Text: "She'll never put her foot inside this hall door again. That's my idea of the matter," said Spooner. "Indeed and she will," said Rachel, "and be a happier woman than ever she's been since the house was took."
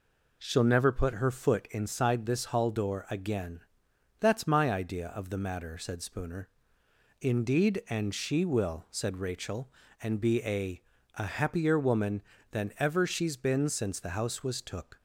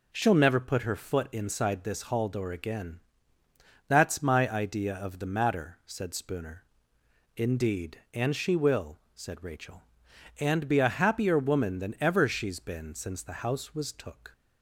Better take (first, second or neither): second